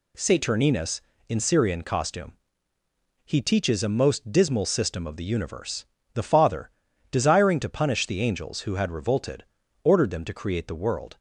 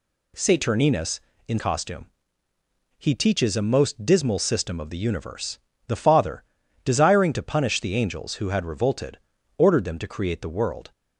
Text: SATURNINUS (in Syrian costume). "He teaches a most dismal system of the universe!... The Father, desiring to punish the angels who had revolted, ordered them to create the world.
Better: first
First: none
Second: skips "Syrian"; at 1.5 s

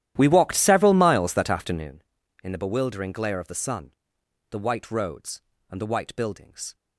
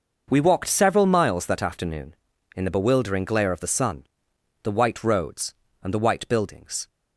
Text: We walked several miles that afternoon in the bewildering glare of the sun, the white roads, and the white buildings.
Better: second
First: starts louder than the rest; strong; until 1.9 s; 12.5 dB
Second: none

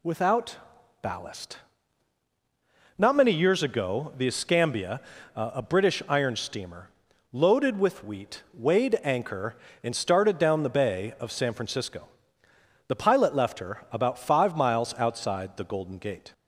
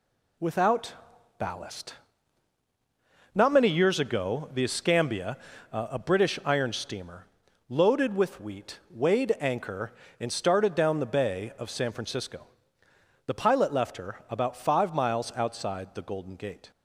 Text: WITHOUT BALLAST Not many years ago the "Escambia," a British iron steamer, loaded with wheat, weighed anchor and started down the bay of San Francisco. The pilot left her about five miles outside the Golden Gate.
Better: first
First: pauses between "WITHOUT" and "BALLAST"; at 0.5 s; 0.44 s long // pauses between "BALLAST" and "Not"; strong; at 1.5 s; 1.4 s long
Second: gets quieter; throughout; 6.5 dB // pauses between "WITHOUT" and "BALLAST"; at 0.9 s; 0.44 s long // pauses between "BALLAST" and "Not"; strong; at 1.9 s; 1.4 s long

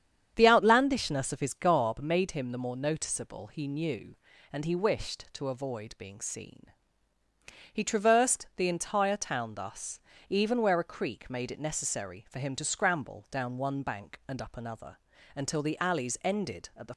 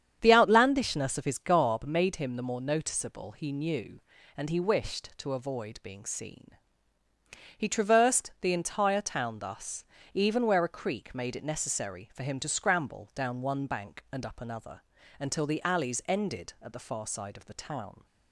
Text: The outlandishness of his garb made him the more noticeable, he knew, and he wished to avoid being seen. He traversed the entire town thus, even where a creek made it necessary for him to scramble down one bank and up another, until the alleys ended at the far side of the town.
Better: second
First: starts louder than the rest; strong; until 1.3 s; 8.5 dB // stops before "far side of the town"; at 16.9 s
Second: starts louder than the rest; strong; until 1.2 s; 8.5 dB

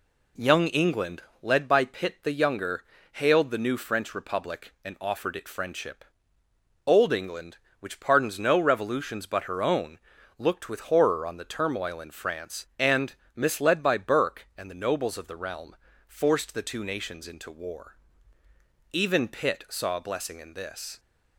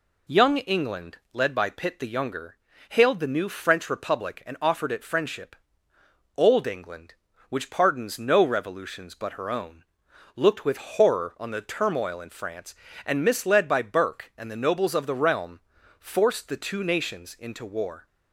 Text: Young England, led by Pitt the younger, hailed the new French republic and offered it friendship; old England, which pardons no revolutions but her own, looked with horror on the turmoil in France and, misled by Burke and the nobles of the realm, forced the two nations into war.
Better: second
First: goes on to say "Even Pitt saw a blessing in this"; strong; from 18.9 s on; 2.0 s long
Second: none

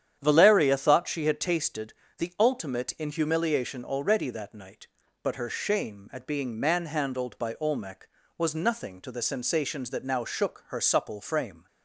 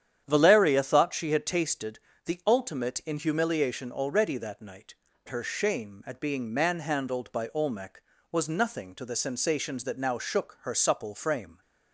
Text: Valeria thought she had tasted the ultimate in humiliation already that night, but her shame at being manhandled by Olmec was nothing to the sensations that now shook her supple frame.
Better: first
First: starts louder than the rest; strong; until 1.2 s; 9.5 dB // pauses between "tasted" and "the"; slight; at 1.9 s; 0.24 s long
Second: starts louder than the rest; strong; until 1.2 s; 9.5 dB // pauses between "tasted" and "the"; slight; at 1.9 s; 0.26 s long // skips "but"; at 5.1 s

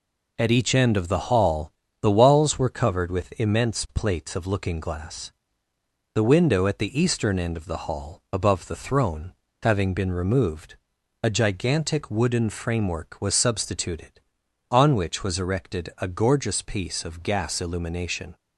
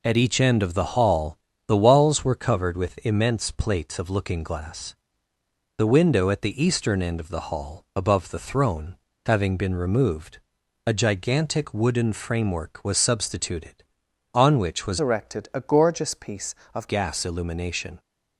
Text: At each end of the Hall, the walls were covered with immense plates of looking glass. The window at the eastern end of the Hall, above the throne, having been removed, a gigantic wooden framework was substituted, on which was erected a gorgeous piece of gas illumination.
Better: first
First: none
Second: changes voice from "erected" to "of"; from 14.9 to 16.8 s; 1.9 s long

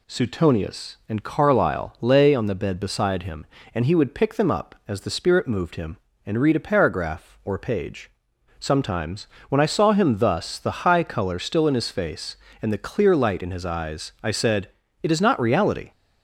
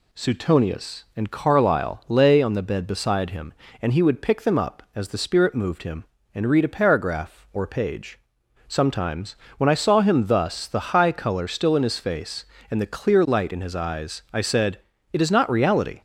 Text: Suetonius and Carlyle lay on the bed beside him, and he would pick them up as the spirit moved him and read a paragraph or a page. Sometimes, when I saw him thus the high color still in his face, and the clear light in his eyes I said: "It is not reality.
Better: neither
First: none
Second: none

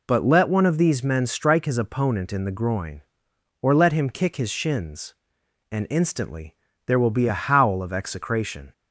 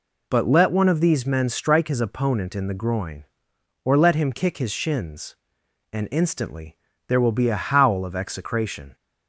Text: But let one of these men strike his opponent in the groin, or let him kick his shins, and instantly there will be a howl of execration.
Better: neither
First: pauses between "instantly" and "there"; slight; at 6.5 s; 0.30 s long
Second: pauses between "instantly" and "there"; slight; at 6.7 s; 0.30 s long

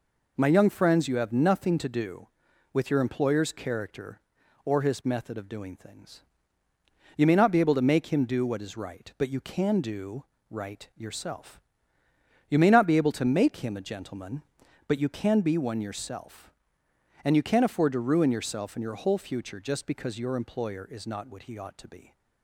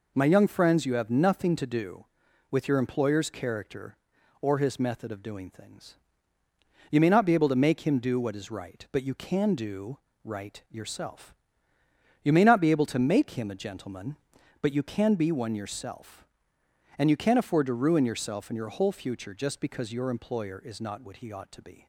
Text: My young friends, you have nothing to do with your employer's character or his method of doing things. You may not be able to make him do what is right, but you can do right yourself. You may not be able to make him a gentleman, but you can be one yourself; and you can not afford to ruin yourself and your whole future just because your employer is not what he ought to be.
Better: neither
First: pauses between "do" and "right"; slight; at 10.2 s; 0.26 s long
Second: pauses between "do" and "right"; slight; at 9.9 s; 0.26 s long

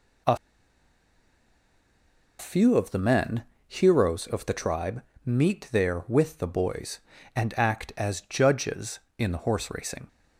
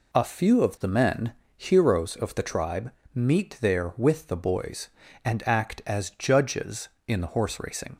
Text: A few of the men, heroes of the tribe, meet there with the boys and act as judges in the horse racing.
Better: second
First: pauses between "A" and "few"; strong; at 0.3 s; 2.0 s long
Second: none

